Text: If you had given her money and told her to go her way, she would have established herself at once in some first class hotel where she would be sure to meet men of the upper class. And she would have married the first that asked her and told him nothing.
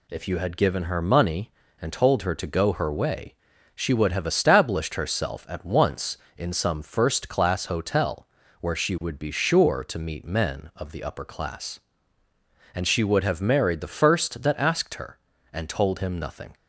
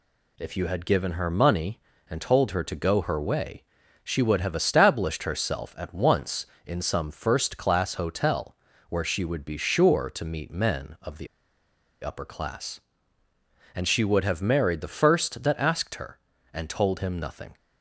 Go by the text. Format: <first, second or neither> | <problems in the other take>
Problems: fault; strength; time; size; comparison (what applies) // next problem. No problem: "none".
first | pauses between "hotel" and "where"; slight; at 8.5 s; 0.34 s long; slight in the first // pauses between "the" and "upper"; noticeable; at 11.2 s; 0.75 s long